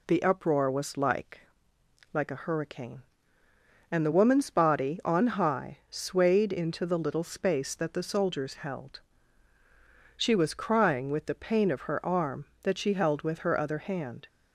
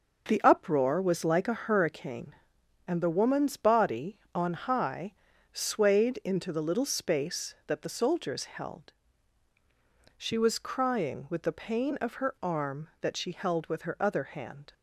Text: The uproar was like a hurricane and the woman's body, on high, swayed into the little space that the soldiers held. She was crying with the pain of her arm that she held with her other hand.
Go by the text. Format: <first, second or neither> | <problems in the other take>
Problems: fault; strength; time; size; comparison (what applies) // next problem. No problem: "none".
second | says "like" twice; at 2.1 s